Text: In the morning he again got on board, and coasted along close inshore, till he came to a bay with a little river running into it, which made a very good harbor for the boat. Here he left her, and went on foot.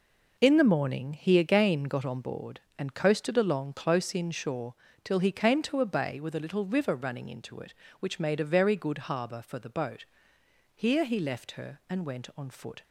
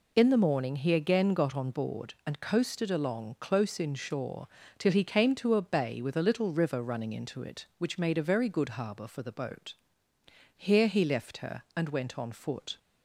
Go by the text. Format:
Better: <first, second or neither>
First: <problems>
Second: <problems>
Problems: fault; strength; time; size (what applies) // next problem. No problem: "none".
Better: neither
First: none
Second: none